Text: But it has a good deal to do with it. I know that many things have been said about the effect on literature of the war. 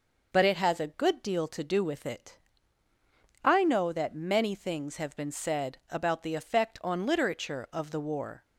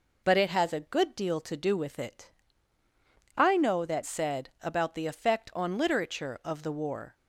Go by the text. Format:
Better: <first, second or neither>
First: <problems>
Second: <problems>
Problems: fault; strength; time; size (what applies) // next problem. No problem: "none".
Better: first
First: none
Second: skips "many things have been"; at 4.0 s